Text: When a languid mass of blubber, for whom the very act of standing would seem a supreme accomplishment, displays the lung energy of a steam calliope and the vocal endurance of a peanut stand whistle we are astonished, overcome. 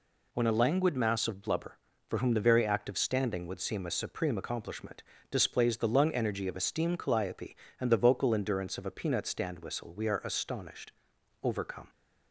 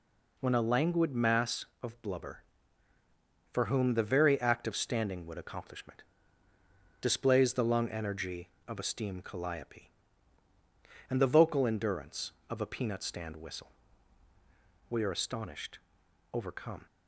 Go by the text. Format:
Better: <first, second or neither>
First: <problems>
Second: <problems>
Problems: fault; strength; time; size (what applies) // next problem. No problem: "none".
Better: first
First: none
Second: skips "seem a supreme"; at 5.3 s // pauses between "whistle" and "we"; at 13.7 s; 1.1 s long